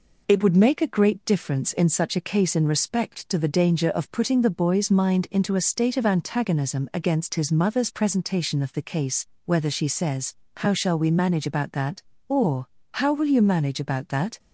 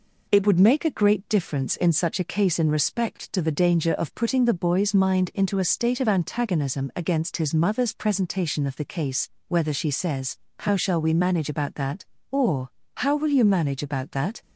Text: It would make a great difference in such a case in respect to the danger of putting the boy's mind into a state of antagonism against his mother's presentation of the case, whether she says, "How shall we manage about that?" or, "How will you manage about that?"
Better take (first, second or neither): neither